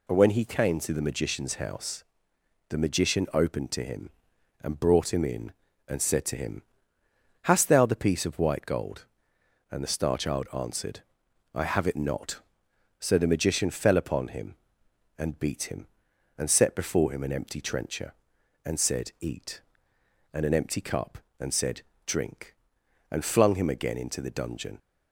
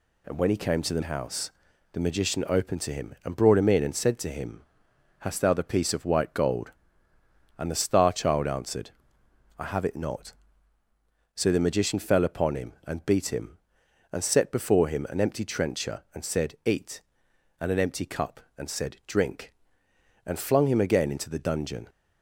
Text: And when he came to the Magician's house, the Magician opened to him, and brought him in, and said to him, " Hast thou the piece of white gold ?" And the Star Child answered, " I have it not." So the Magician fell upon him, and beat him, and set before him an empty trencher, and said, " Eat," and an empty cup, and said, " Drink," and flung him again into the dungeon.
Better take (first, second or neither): first